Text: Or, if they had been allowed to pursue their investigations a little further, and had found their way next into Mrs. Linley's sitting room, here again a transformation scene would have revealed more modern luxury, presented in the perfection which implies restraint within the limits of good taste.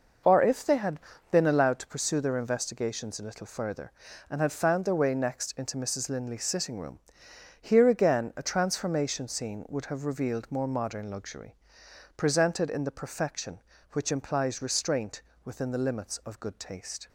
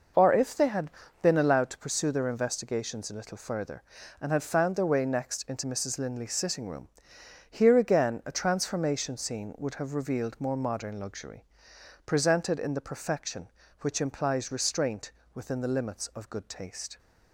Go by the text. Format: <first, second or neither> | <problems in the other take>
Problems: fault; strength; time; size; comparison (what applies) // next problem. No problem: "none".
neither | pauses between "had" and "been"; slight; the same in both // pauses between "restraint" and "within"; slight; the same in both